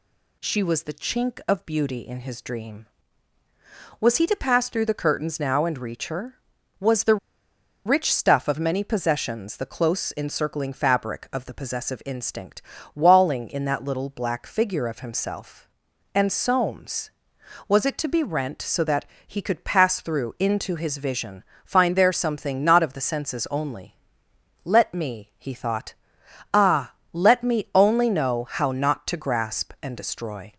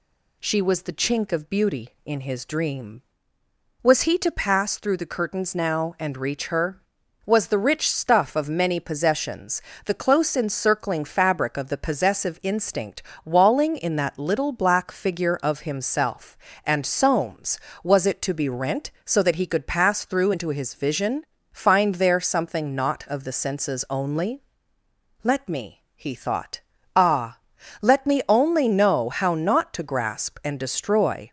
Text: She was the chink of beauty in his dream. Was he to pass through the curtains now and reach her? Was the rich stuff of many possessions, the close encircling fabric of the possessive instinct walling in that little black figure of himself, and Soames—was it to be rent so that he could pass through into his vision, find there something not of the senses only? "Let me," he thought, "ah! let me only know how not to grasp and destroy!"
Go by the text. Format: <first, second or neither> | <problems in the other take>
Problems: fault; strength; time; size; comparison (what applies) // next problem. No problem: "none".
second | pauses between "the" and "rich"; noticeable; at 7.1 s; 0.69 s long // pauses between "instinct" and "walling"; slight; at 12.6 s; 0.32 s long; slight in the second // pauses between "that" and "he"; slight; at 19.0 s; 0.22 s long